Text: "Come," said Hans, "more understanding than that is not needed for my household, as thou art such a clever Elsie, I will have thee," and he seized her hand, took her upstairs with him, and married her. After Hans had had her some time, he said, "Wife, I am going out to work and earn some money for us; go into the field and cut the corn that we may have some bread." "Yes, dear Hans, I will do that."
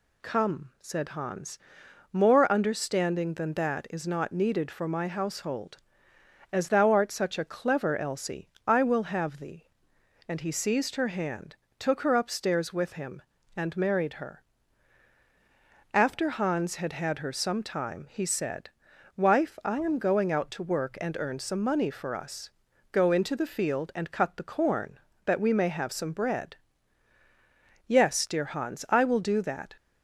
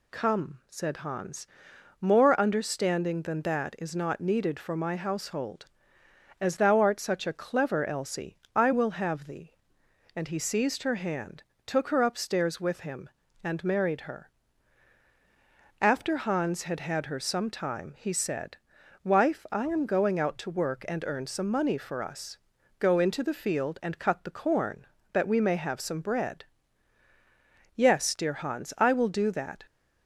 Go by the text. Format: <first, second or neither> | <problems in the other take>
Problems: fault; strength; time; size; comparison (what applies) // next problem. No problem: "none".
neither | none